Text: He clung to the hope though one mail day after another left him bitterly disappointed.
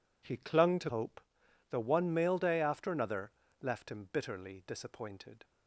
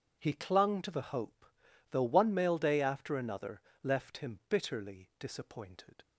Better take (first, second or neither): second